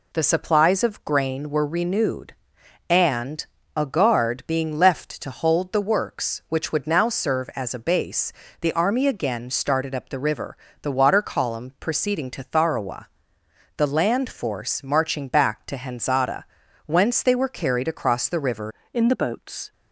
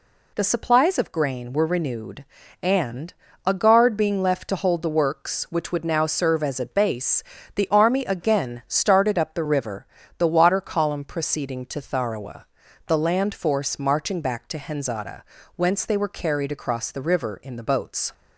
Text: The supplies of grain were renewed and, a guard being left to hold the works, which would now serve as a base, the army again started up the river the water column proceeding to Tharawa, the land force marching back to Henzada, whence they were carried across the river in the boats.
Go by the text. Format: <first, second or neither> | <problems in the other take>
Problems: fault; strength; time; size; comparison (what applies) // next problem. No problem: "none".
second | pauses between "river" and "the"; slight; at 10.5 s; 0.24 s long; slight in the second // changes voice at "in"; from 18.9 s on; 0.8 s long